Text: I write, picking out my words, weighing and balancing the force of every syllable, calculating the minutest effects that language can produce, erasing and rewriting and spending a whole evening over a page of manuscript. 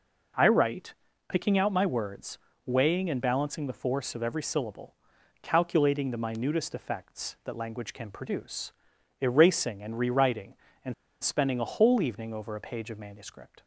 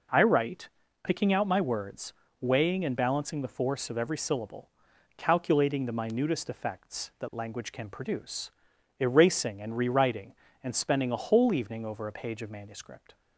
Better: second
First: pauses between "and" and "spending"; slight; at 10.9 s; 0.29 s long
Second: none

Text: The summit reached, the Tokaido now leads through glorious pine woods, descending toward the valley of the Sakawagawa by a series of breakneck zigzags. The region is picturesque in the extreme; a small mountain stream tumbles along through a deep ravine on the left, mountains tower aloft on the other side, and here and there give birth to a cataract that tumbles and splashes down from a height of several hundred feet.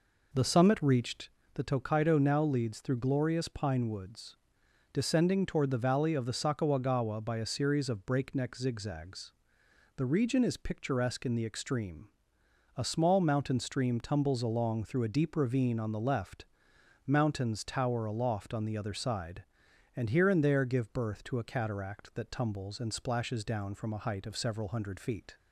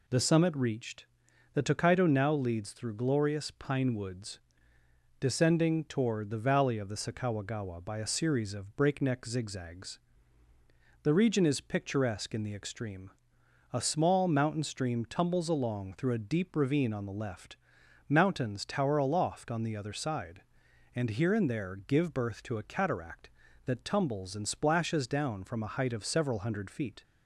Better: second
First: starts louder than the rest; noticeable; until 1.3 s; 4 dB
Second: none

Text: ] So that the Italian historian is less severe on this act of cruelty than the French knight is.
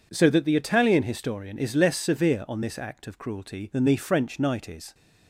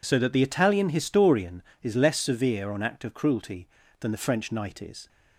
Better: first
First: none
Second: skips "this"; at 2.8 s

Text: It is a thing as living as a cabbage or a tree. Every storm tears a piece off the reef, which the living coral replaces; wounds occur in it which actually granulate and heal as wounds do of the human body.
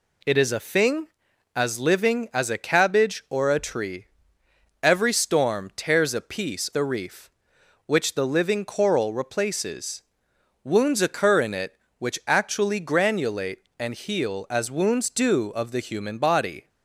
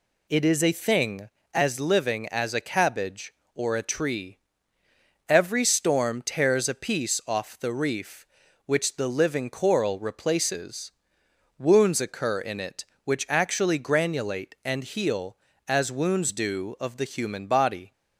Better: second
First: skips "off"; at 6.7 s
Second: none

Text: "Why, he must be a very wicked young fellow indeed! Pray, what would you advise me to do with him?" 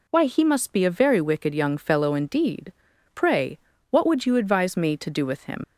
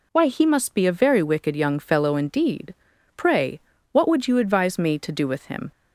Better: second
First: leaves "him" unfinished; at 5.6 s; 50 ms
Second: none

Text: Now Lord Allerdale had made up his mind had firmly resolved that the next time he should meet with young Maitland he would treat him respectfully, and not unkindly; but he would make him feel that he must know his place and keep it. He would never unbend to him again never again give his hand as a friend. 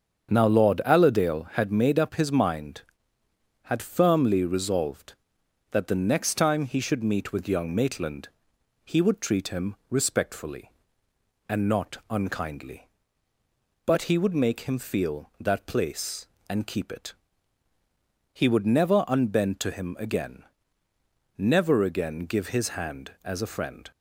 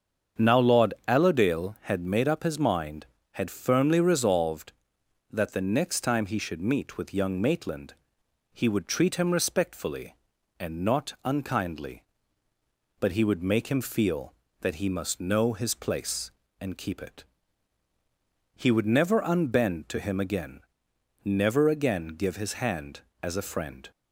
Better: second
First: starts louder than the rest; strong; until 1.3 s; 7.5 dB // pauses between "Maitland" and "he"; noticeable; at 8.2 s; 0.56 s long // pauses between "him" and "respectfully"; slight; at 9.7 s; 0.16 s long // skips "he must know his"; at 15.6 s // pauses between "again" and "never"; noticeable; at 20.4 s; 0.96 s long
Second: starts louder than the rest; strong; until 1.5 s; 7 dB // pauses between "Maitland" and "he"; noticeable; at 7.9 s; 0.62 s long // pauses between "again" and "never"; noticeable; at 20.6 s; 0.62 s long

